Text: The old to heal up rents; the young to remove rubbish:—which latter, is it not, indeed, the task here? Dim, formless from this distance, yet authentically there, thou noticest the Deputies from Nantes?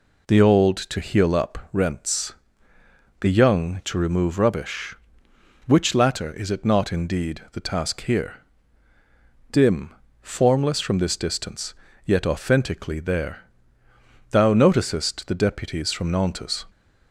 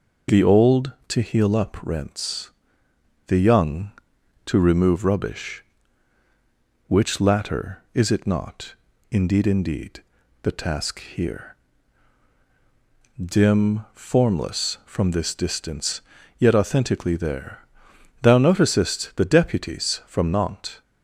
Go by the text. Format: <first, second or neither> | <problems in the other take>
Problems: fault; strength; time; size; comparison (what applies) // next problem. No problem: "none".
first | says "indeed" twice; at 9.4 s